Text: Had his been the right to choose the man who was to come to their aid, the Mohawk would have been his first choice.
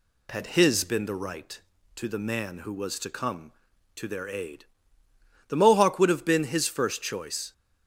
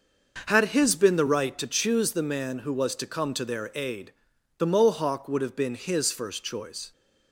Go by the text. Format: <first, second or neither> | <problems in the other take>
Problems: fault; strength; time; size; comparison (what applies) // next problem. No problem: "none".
second | skips "choose"; at 2.0 s